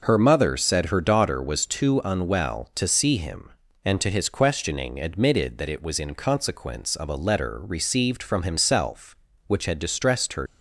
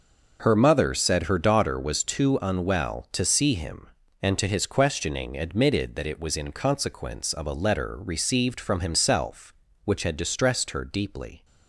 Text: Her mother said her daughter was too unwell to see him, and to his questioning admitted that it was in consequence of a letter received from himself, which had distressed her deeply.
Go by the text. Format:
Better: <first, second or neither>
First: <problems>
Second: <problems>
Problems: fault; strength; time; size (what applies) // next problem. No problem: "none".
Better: second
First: starts louder than the rest; noticeable; until 1.0 s; 6 dB // stops before "deeply"; at 10.4 s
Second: starts louder than the rest; noticeable; until 1.4 s; 6 dB